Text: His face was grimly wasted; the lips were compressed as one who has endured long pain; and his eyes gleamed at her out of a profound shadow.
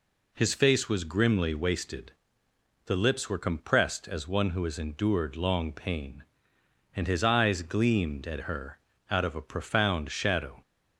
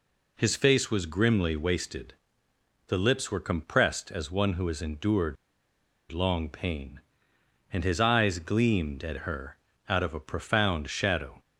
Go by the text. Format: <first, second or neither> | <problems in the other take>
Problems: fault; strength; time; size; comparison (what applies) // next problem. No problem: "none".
first | pauses between "endured" and "long"; noticeable; at 5.3 s; 0.76 s long // pauses between "her" and "out"; slight; at 9.5 s; 0.32 s long; slight in the first